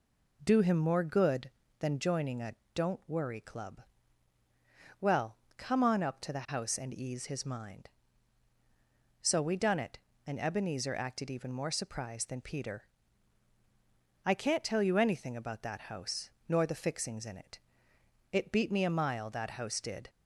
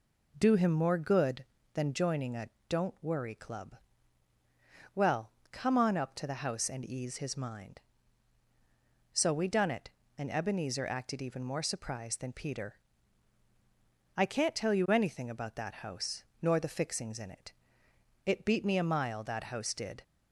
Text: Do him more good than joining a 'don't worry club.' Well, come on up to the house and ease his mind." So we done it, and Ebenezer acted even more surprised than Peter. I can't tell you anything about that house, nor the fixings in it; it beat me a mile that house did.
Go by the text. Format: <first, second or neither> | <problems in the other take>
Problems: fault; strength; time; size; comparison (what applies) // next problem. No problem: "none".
neither | pauses between "a" and "don't"; slight; the same in both